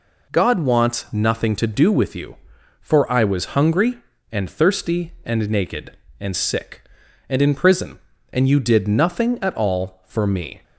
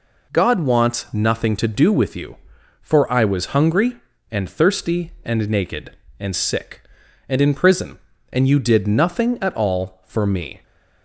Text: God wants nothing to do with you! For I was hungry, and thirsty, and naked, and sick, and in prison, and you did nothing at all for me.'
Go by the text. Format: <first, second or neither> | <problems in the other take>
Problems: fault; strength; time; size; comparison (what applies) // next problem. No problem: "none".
neither | none